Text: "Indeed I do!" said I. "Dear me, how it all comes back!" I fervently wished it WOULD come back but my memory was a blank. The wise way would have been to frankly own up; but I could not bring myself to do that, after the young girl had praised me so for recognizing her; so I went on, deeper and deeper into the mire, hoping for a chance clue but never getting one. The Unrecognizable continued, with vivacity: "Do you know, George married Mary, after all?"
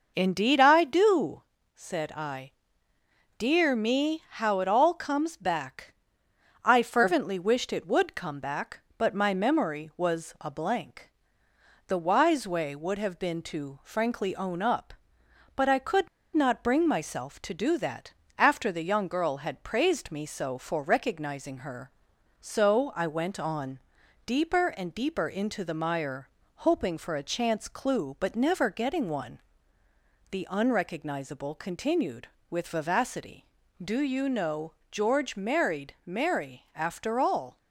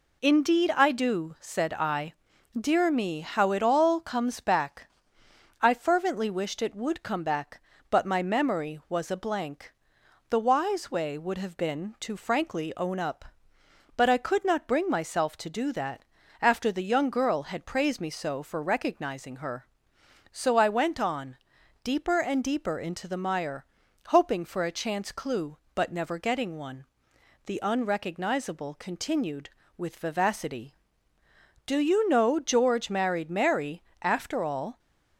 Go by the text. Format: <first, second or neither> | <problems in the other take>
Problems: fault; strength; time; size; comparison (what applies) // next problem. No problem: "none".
second | pauses between "could" and "not"; slight; at 16.0 s; 0.26 s long